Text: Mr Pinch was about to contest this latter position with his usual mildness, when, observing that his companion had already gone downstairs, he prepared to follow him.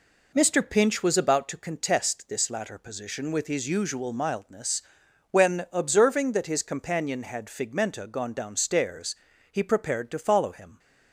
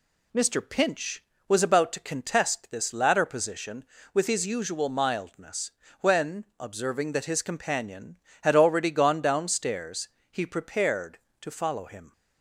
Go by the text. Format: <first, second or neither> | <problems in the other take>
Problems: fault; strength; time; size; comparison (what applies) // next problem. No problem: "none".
second | says "figmenta" for "already"; at 7.4 s